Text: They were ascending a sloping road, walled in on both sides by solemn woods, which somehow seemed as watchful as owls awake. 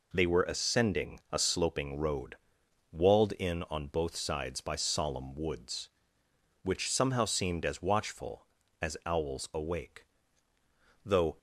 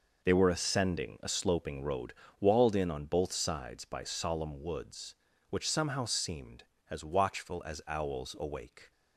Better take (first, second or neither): second